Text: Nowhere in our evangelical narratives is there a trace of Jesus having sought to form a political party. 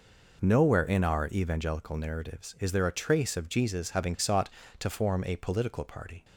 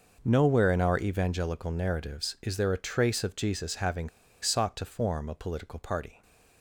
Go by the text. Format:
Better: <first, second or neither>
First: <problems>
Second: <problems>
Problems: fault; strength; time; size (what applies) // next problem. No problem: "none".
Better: first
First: none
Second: pauses between "having" and "sought"; slight; at 4.0 s; 0.32 s long